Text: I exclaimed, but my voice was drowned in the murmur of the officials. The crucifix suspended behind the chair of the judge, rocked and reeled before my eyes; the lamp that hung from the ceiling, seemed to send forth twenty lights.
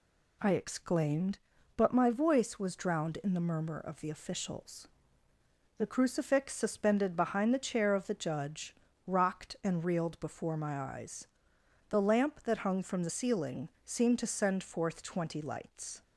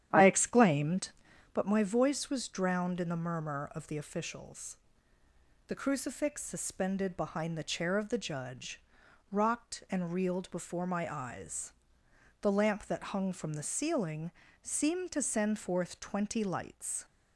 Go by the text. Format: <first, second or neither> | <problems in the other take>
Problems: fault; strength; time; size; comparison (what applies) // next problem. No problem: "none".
first | starts louder than the rest; strong; until 1.7 s; 10.5 dB